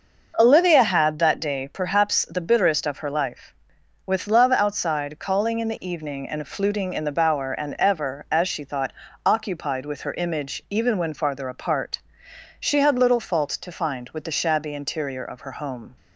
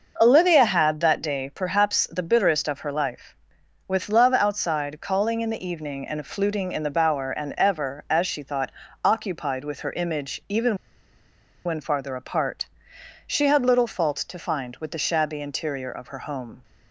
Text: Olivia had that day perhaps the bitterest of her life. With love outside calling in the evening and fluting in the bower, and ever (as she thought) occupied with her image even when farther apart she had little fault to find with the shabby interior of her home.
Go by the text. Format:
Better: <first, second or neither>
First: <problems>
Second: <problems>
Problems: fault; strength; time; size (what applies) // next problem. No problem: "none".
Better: first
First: pauses between "apart" and "she"; noticeable; at 11.9 s; 0.62 s long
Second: pauses between "even" and "when"; noticeable; at 10.7 s; 0.91 s long // pauses between "apart" and "she"; noticeable; at 12.6 s; 0.62 s long